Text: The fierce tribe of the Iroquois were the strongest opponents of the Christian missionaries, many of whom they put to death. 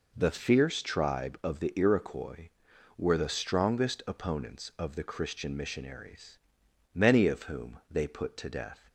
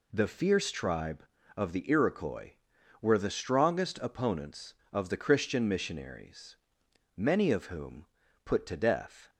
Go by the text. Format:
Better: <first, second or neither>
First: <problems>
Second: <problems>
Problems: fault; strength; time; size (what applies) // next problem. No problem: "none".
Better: first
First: none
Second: skips "they"; at 8.2 s